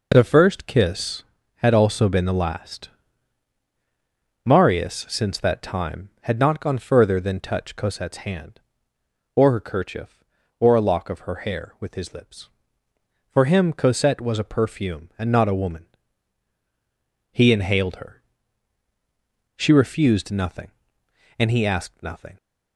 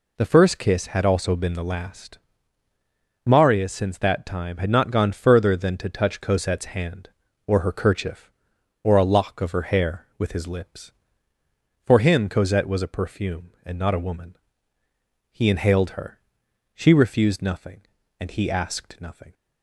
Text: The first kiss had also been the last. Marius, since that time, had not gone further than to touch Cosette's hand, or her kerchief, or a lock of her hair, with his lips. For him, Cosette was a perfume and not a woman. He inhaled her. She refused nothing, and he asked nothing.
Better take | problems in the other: second | skips "to"; at 7.4 s

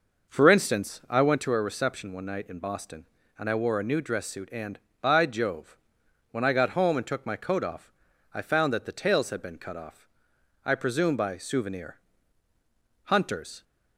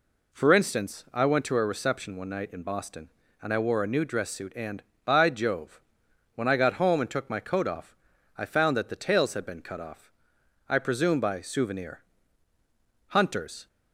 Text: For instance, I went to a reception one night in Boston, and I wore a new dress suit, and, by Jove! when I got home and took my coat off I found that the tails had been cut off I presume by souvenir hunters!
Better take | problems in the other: second | starts louder than the rest; noticeable; until 1.5 s; 5.5 dB // pauses between "off" and "I"; at 7.9 s; 0.44 s long; also in the second // pauses between "off" and "I"; noticeable; at 10.0 s; 0.56 s long; noticeable in the second // pauses between "souvenir" and "hunters"; at 11.9 s; 1.0 s long; also in the second

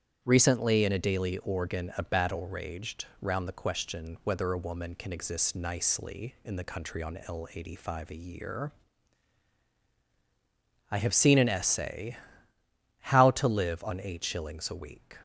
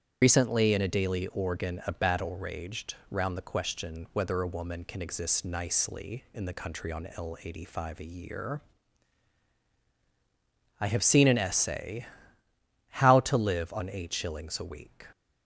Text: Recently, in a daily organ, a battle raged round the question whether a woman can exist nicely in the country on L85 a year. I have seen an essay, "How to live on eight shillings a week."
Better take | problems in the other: first | loses the start of "Recently"; at 0.2 s; 90 ms // starts louder than the rest; strong; until 1.2 s; 8.5 dB; strong in the first

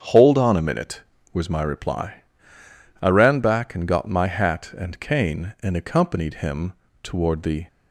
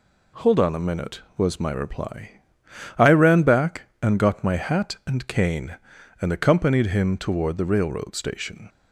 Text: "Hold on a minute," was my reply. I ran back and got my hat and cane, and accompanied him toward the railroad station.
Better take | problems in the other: second | starts louder than the rest; strong; until 1.4 s; 7.5 dB // pauses between "him" and "toward"; slight; at 6.7 s; 0.30 s long // stops before "railroad station"; at 7.6 s

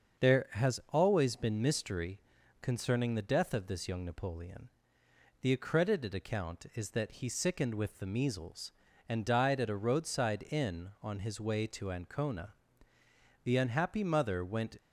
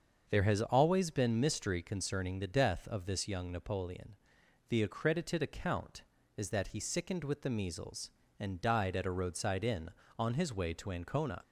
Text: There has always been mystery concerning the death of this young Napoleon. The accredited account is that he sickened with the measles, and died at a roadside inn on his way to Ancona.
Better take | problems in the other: second | starts louder than the rest; until 1.3 s; 6.5 dB; also in the second // pauses between "mystery" and "concerning"; at 2.1 s; 0.42 s long // goes on to say "The unhappy mother went"; from 13.4 s on; 1.3 s long

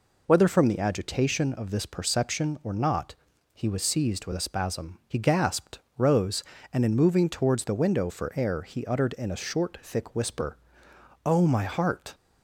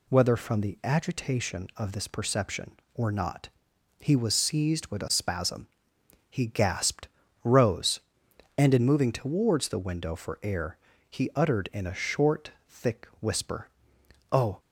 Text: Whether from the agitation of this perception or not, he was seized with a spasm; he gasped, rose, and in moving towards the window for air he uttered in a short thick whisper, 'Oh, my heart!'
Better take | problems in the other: first | pauses between "air" and "he"; slight; at 10.7 s; 0.30 s long // pauses between "short" and "thick"; slight; at 12.4 s; 0.18 s long // stops before "my heart"; at 14.6 s

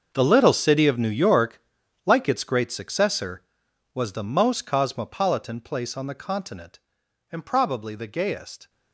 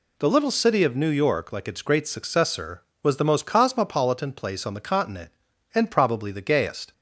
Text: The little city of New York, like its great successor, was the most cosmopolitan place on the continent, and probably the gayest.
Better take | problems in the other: second | gets quieter; strong; throughout; 15.5 dB

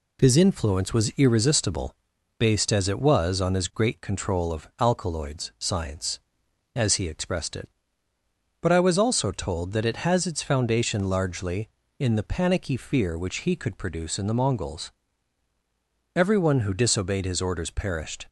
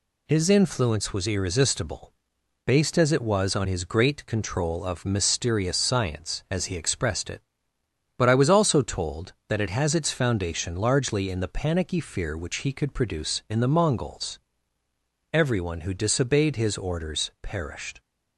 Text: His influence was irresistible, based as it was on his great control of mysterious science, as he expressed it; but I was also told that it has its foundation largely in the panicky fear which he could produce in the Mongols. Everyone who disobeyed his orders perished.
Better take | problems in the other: second | says "alkaloids" for "mysterious"; at 4.7 s

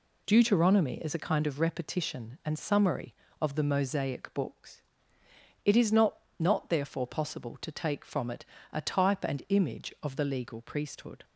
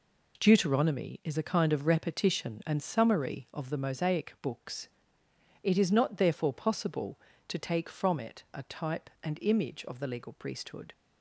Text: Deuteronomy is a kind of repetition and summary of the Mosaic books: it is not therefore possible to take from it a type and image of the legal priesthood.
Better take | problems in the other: second | says "not" twice; at 6.3 s // pauses between "it" and "a"; slight; at 8.4 s; 0.28 s long

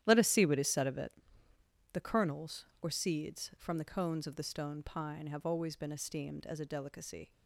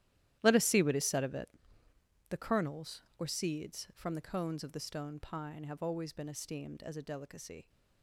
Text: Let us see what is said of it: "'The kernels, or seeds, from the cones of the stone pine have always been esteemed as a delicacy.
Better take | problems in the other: first | gets quieter; strong; throughout; 15.5 dB // starts louder than the rest; strong; until 1.4 s; 13.5 dB; strong in the first

